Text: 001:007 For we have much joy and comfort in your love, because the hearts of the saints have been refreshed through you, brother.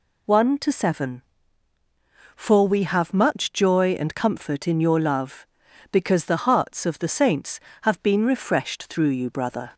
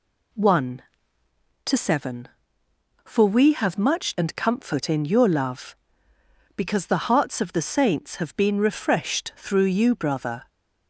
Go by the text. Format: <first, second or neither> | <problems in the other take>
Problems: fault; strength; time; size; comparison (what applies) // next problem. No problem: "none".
first | skips "joy"; at 4.1 s